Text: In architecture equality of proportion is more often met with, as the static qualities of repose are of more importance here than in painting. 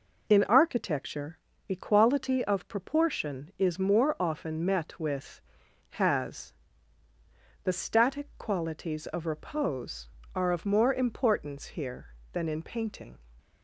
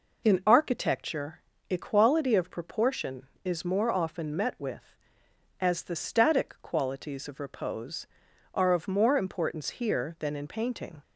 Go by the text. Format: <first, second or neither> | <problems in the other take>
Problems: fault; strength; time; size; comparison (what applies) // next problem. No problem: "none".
second | pauses between "architecture" and "equality"; slight; at 1.3 s; 0.32 s long; slight in the second // says "has" for "as"; at 5.9 s